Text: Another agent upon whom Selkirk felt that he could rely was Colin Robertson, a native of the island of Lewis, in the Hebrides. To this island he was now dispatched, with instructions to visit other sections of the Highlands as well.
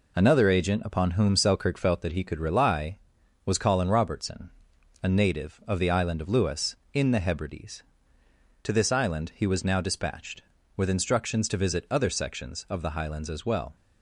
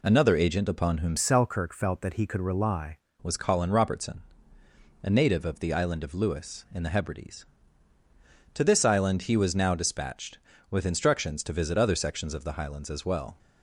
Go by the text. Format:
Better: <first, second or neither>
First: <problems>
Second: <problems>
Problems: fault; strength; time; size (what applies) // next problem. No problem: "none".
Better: first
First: none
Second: changes voice from "Selkirk" to "rely"; from 1.1 to 2.9 s; 1.8 s long